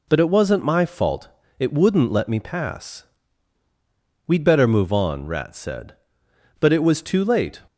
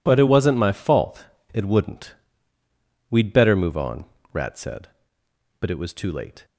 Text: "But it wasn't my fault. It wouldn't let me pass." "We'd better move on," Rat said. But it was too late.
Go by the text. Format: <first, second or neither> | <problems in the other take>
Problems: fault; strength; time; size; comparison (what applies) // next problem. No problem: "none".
first | skips "let me pass"; at 2.6 s